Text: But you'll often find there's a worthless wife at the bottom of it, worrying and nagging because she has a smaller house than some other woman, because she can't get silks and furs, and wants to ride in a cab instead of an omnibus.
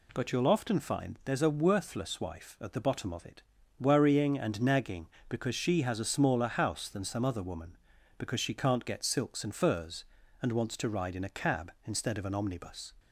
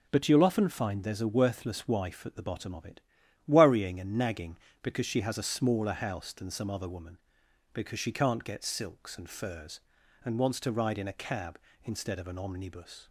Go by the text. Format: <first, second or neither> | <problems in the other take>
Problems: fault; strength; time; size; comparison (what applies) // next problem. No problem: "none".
neither | none